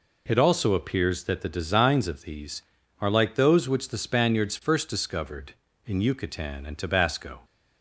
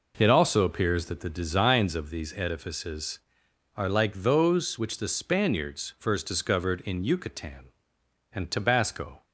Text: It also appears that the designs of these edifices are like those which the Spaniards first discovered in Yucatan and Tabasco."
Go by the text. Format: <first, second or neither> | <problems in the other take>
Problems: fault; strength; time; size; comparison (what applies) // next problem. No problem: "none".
second | skips "edifices"; at 2.8 s